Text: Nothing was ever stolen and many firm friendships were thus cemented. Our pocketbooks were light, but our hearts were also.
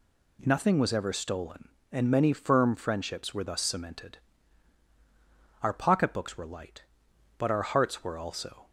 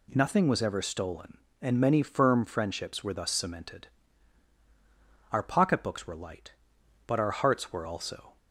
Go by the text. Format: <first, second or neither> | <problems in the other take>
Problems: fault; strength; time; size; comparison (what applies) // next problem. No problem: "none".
neither | none